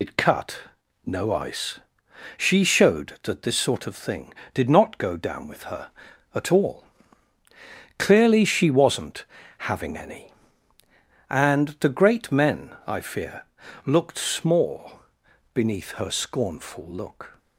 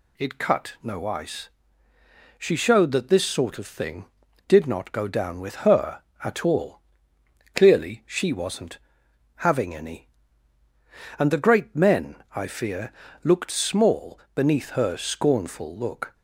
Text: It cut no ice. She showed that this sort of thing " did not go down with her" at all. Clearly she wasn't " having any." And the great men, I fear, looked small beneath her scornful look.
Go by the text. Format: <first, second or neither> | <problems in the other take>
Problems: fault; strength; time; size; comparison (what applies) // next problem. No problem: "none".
second | loses the start of "It"; at 0.0 s; 70 ms // pauses between "cut" and "no"; noticeable; at 0.5 s; 0.46 s long // pauses between "small" and "beneath"; noticeable; at 14.9 s; 0.52 s long; slight in the second